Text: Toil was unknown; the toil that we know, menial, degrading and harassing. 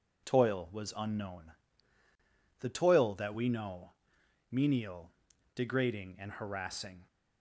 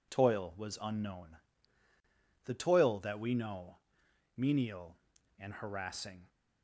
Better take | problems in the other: first | skips "degrading"; at 5.1 s

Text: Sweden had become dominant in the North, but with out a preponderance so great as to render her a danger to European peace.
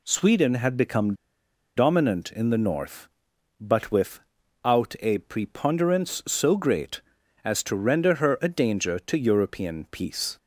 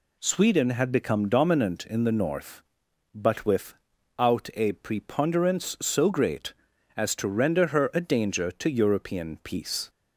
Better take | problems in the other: second | pauses between "become" and "dominant"; noticeable; at 1.1 s; 0.62 s long // pauses between "with" and "out"; at 4.1 s; 0.44 s long; also in the second

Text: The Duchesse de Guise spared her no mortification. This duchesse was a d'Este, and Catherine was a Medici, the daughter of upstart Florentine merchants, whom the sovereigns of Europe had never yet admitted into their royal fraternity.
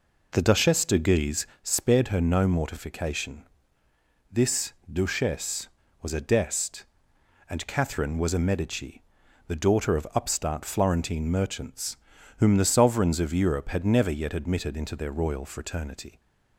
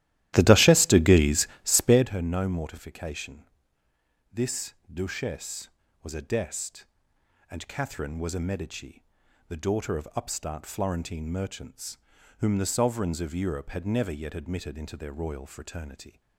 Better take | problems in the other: first | starts louder than the rest; strong; until 2.2 s; 14 dB // pauses between "Guise" and "spared"; slight; at 1.4 s; 0.16 s long; slight in the first // pauses between "This" and "duchesse"; slight; at 4.7 s; 0.18 s long; slight in the first

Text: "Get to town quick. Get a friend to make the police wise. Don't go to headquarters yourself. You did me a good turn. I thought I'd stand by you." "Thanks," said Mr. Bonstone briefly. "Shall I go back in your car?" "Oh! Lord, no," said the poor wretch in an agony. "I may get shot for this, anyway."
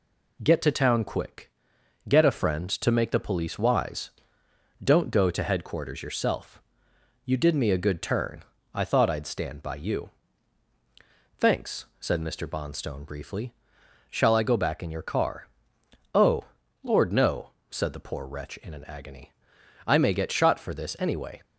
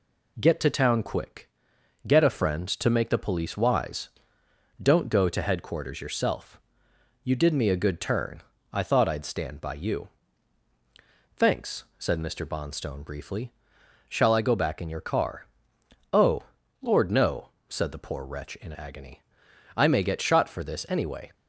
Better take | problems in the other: first | skips "an"; at 18.7 s

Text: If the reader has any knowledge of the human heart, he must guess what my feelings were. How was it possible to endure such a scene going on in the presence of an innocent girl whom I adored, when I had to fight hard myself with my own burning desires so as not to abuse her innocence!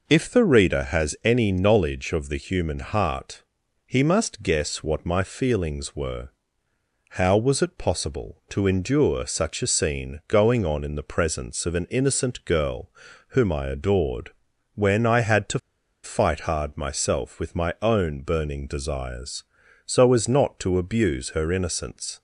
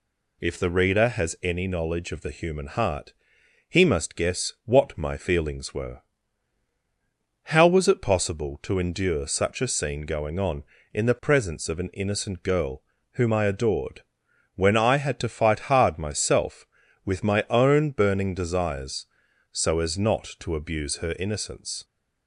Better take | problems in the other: second | pauses between "girl" and "whom"; at 12.9 s; 0.38 s long; slight in the second // pauses between "to" and "fight"; at 15.5 s; 0.44 s long

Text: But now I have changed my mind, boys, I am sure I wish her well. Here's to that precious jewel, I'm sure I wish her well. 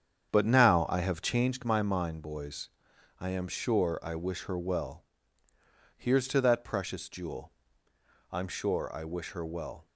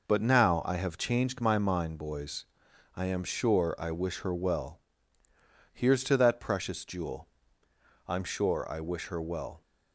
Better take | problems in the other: second | starts louder than the rest; strong; until 1.6 s; 8 dB

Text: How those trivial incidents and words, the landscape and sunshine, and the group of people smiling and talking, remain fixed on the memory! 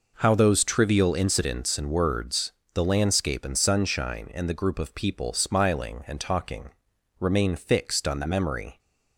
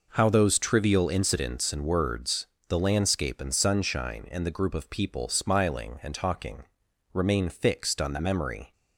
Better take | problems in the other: neither | none

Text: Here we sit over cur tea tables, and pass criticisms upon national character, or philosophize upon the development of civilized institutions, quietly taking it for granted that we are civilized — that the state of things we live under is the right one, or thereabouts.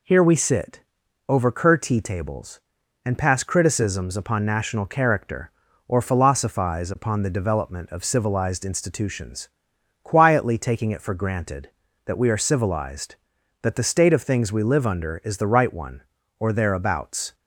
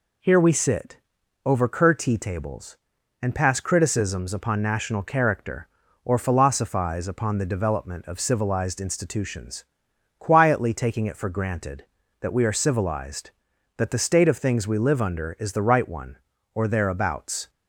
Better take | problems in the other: neither | pauses between "sit" and "over"; noticeable; the same in both

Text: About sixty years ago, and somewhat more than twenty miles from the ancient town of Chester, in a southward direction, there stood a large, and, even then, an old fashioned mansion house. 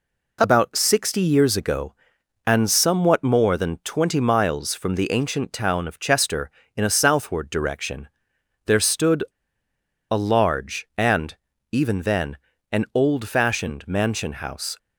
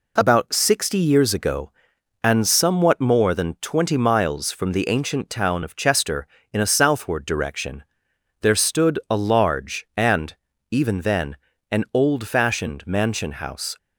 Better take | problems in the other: second | pauses between "stood" and "a"; noticeable; at 9.2 s; 0.90 s long

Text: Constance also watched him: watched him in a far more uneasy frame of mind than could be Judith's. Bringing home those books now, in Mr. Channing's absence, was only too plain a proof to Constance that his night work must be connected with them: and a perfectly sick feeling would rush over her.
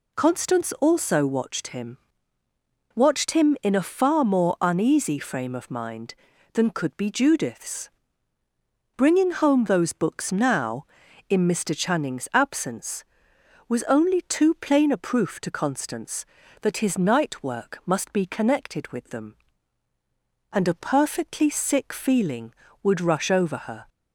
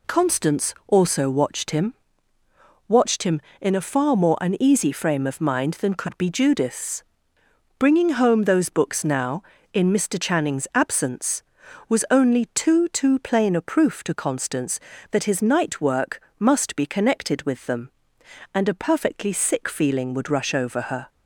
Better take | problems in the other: first | says "too" twice; at 12.8 s // pauses between "work" and "must"; slight; at 16.2 s; 0.18 s long

